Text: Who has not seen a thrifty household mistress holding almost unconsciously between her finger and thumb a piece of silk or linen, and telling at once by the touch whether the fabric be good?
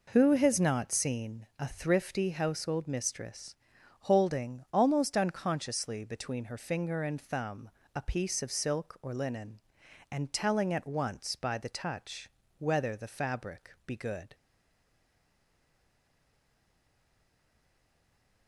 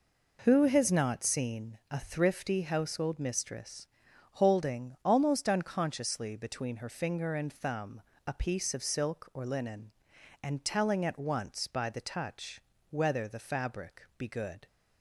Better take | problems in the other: second | pauses between "mistress" and "holding"; noticeable; at 3.5 s; 0.46 s long; noticeable in the second // pauses between "thumb" and "a"; slight; at 7.6 s; 0.26 s long; slight in the second // pauses between "touch" and "whether"; slight; at 12.3 s; 0.26 s long; slight in the second // stays silent after the last word; strong; from 14.3 s on; 4.1 s long

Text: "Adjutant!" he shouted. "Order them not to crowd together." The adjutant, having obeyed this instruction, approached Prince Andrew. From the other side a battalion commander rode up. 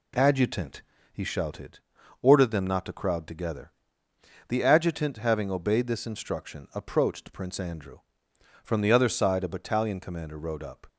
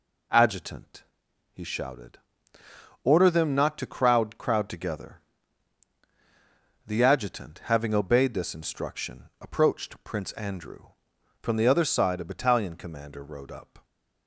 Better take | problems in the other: first | says "crowd" twice; at 4.3 s

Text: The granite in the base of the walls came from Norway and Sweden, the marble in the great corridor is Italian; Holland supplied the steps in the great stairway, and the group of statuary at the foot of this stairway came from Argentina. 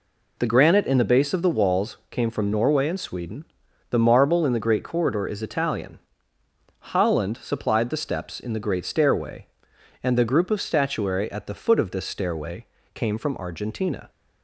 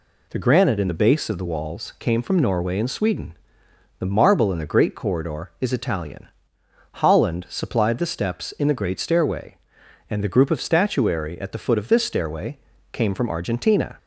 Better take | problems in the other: neither | pauses between "stairway" and "came"; slight; the same in both

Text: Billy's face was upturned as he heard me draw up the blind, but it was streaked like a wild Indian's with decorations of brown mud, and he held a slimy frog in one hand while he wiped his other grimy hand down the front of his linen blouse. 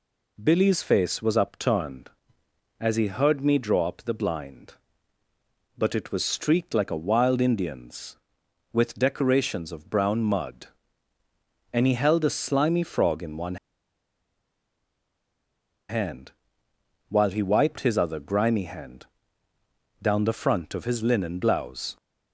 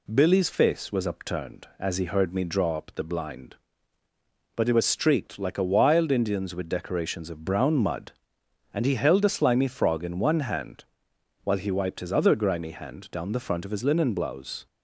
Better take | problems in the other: second | pauses between "one" and "hand"; strong; at 13.5 s; 2.3 s long // pauses between "hand" and "while"; noticeable; at 16.3 s; 0.78 s long; noticeable in the second // pauses between "hand" and "down"; noticeable; at 19.0 s; 0.96 s long

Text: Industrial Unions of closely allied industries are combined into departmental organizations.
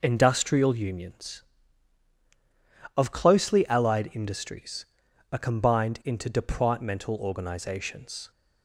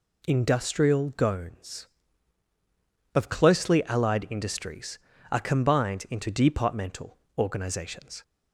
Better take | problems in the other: first | says "Gones" for "Unions"; at 1.1 s // pauses between "departmental" and "organizations"; slight; at 7.1 s; 0.22 s long

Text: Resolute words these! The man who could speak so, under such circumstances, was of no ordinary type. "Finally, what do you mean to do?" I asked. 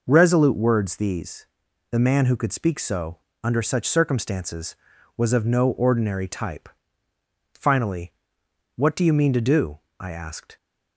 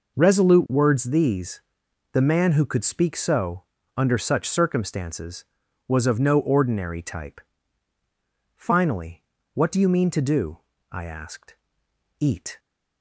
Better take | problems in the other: first | goes on to say "Eat"; slight; from 12.1 s on; 0.40 s long

